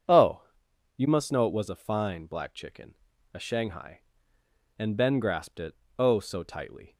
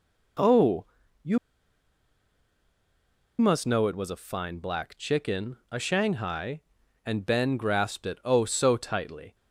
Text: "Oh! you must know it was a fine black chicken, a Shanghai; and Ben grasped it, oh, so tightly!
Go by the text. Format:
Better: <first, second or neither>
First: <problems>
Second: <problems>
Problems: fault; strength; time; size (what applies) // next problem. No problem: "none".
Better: first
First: none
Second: pauses between "you" and "must"; strong; at 1.3 s; 2.0 s long